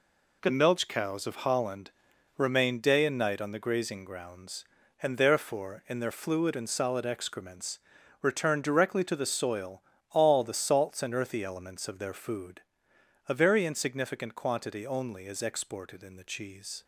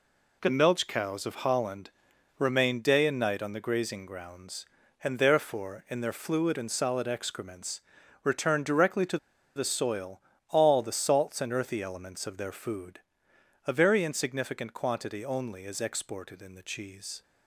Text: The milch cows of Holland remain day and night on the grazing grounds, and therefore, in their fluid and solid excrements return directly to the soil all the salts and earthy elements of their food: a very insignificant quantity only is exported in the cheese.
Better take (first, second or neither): first